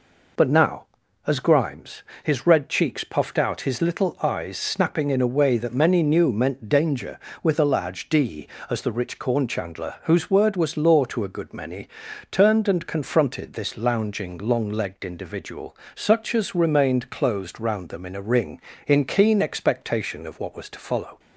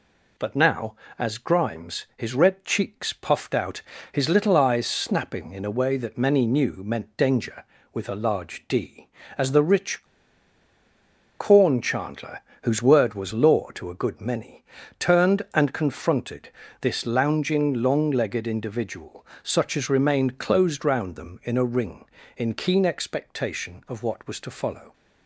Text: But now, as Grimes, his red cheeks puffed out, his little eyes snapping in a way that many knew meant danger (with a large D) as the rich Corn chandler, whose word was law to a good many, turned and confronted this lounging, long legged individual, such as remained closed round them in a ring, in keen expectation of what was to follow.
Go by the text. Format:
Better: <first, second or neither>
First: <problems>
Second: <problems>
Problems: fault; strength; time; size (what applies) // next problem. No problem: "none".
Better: first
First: none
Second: pauses between "rich" and "Corn"; strong; at 10.0 s; 1.3 s long // pauses between "confronted" and "this"; slight; at 16.4 s; 0.32 s long